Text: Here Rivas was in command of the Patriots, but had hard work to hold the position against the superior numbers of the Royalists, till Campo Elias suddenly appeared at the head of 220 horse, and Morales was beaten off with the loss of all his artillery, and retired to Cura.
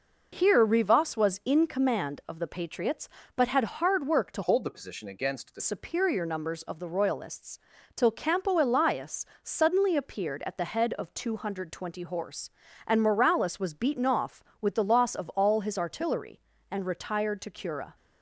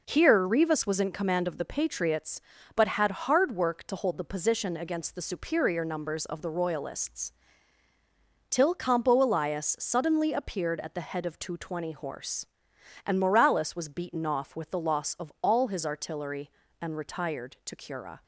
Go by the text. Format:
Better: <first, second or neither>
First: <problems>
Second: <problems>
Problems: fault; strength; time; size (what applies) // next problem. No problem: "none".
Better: second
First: changes voice from "hold" to "the"; from 4.4 to 5.6 s; 1.2 s long // pauses between "Elias" and "suddenly"; slight; at 9.2 s; 0.18 s long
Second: none